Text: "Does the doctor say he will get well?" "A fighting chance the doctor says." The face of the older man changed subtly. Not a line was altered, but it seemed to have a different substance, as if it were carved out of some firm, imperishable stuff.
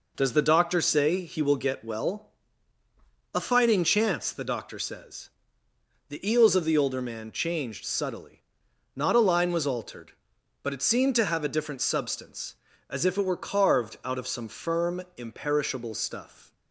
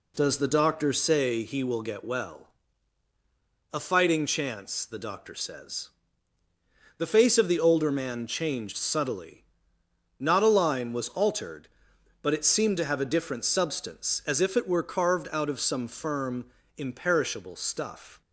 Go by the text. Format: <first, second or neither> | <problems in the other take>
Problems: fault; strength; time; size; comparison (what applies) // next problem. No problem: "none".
second | says "eels" for "face"; at 6.3 s